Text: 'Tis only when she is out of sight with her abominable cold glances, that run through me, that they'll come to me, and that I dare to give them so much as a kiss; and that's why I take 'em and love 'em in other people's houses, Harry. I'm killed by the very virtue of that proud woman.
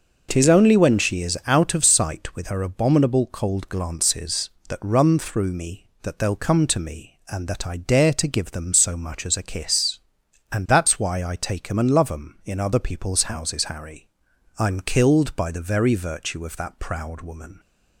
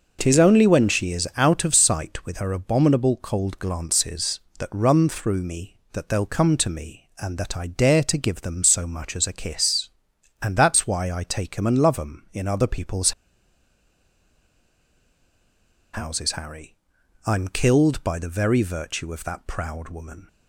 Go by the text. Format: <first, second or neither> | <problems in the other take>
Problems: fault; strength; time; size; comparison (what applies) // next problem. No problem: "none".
first | pauses between "people's" and "houses"; strong; at 13.1 s; 2.8 s long